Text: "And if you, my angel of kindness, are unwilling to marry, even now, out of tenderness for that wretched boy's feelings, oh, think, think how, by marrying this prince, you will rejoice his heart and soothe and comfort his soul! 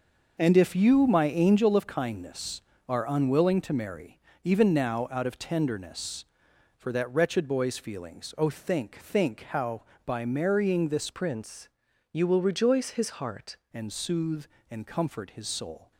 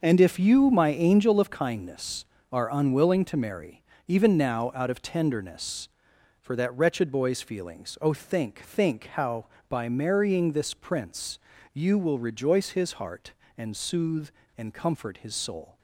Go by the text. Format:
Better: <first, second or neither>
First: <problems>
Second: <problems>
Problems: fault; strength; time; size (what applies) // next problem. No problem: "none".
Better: second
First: starts louder than the rest; noticeable; until 1.3 s; 6 dB // changes voice from "prince" to "heart"; from 11.1 to 13.5 s; 2.4 s long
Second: starts louder than the rest; noticeable; until 1.0 s; 6 dB